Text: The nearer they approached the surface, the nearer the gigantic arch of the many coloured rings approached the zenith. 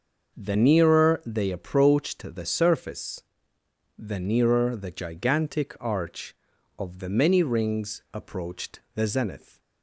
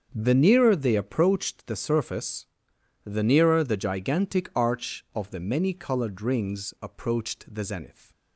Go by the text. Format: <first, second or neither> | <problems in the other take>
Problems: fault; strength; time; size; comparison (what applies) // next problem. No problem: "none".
second | starts louder than the rest; until 1.4 s; 6 dB; also in the second // skips "coloured"; at 7.4 s